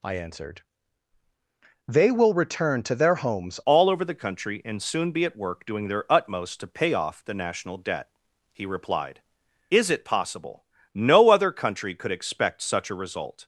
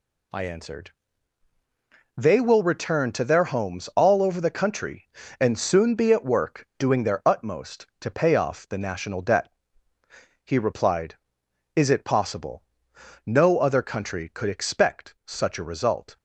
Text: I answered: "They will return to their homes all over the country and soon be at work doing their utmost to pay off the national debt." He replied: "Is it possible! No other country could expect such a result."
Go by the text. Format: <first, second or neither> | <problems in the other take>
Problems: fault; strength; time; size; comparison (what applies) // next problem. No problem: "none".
second | changes voice at "all"; from 3.6 s on; 9.8 s long